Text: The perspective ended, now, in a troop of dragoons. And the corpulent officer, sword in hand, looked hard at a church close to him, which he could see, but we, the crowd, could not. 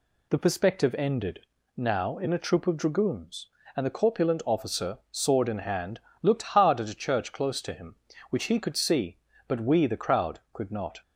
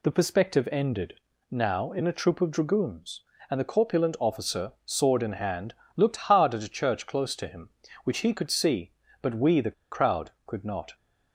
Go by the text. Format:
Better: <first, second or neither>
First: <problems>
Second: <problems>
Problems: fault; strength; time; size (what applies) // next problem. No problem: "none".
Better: first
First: none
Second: pauses between "the" and "crowd"; slight; at 9.7 s; 0.20 s long